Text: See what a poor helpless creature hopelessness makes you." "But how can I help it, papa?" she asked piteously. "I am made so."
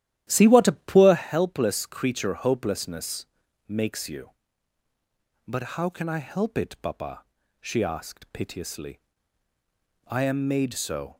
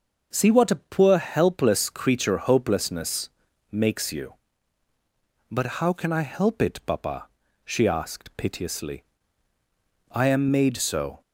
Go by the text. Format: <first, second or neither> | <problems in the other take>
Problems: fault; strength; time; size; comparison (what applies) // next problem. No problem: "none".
second | starts louder than the rest; strong; until 1.3 s; 12.5 dB // pauses between "hopelessness" and "makes"; at 3.2 s; 0.42 s long; also in the second